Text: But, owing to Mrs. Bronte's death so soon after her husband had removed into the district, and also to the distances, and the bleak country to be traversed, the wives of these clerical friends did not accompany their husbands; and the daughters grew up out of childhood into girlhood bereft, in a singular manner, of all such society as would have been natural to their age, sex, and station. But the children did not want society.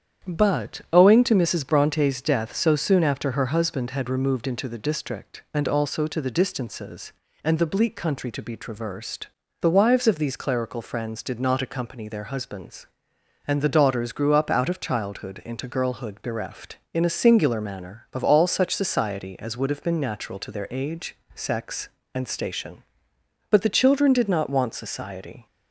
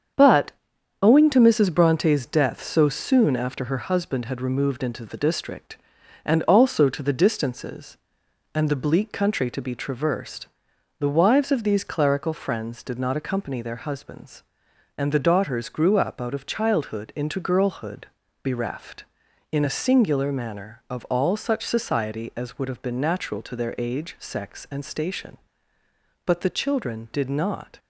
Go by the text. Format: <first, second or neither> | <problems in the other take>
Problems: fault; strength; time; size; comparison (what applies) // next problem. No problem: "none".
first | starts louder than the rest; strong; until 1.6 s; 7.5 dB; strong in the first // pauses between "girlhood" and "bereft"; slight; at 18.0 s; 0.36 s long // stops before "want society"; at 27.7 s